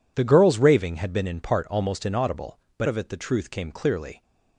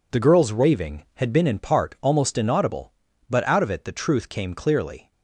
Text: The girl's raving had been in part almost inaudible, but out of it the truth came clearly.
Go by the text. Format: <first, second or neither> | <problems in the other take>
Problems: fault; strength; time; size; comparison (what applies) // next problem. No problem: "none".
second | skips "out"; at 2.8 s